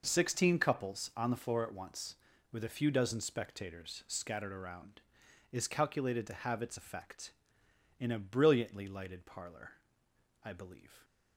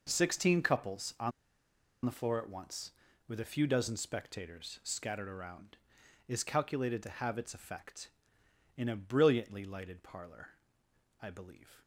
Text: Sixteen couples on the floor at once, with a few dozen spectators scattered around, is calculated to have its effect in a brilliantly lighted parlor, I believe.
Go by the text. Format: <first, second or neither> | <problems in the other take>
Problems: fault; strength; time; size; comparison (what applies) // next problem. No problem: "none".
first | pauses between "on" and "the"; noticeable; at 1.3 s; 0.74 s long